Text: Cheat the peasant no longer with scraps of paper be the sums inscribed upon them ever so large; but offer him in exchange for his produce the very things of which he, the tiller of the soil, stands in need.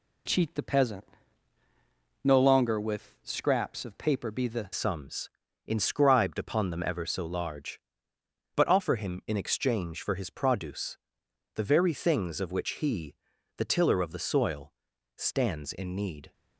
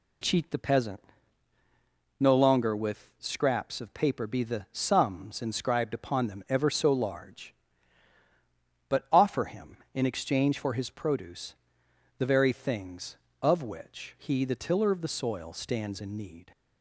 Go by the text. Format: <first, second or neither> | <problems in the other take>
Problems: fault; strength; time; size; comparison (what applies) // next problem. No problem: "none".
second | pauses between "peasant" and "no"; at 1.0 s; 1.2 s long; also in the second // changes voice at "sums"; from 4.7 s on; 11.6 s long // pauses between "sums" and "inscribed"; slight; at 5.3 s; 0.34 s long // pauses between "produce" and "the"; noticeable; at 10.9 s; 0.56 s long; noticeable in the second